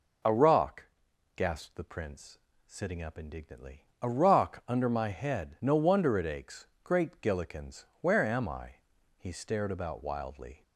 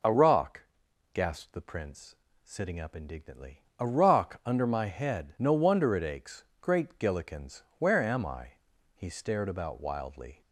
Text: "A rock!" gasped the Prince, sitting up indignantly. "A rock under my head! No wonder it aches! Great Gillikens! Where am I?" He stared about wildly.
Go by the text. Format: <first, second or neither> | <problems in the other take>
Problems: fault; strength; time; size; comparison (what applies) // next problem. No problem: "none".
neither | none